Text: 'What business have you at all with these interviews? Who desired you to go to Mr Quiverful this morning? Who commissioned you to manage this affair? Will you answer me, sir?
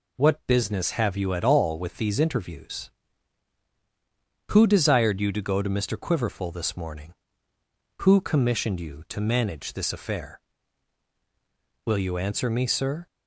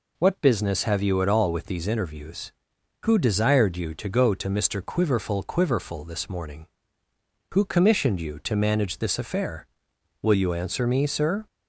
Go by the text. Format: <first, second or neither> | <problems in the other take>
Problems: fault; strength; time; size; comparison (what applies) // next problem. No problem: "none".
first | says "Quiverful" twice; at 5.4 s